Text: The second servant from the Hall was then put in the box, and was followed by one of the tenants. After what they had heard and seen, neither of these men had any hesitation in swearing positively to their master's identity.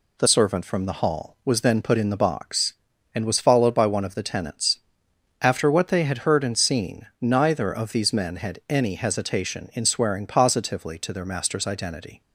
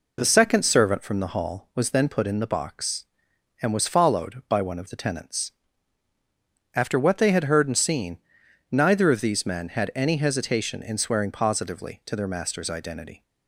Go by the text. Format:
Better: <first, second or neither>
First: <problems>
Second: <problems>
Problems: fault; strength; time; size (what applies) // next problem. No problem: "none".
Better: second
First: skips "second"; at 0.2 s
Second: none